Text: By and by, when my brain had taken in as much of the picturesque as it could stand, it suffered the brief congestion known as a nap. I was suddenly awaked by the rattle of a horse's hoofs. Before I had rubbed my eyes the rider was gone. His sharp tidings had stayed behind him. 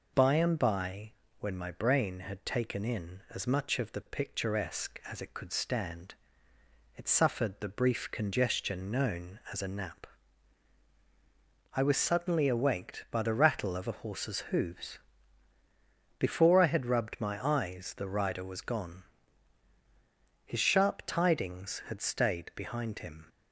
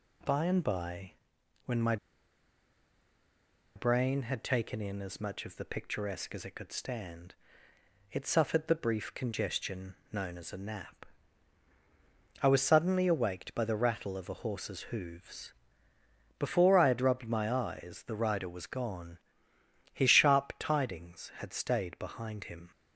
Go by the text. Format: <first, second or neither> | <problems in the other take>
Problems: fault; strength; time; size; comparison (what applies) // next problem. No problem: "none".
first | pauses between "my" and "brain"; strong; at 1.9 s; 1.8 s long // pauses between "congestion" and "known"; slight; at 9.9 s; 0.18 s long